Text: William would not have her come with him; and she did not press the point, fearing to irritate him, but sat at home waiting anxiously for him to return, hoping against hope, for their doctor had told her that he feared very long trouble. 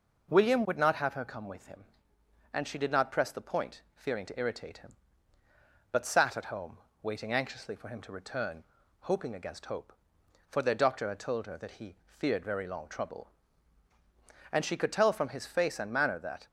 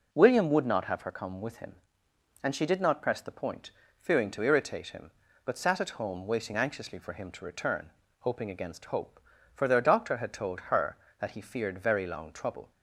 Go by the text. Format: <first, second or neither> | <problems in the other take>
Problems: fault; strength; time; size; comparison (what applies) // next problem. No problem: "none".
second | pauses between "home" and "waiting"; slight; at 6.7 s; 0.26 s long // goes on to say "And she could tell from his face and manner that"; strong; from 14.5 s on; 1.9 s long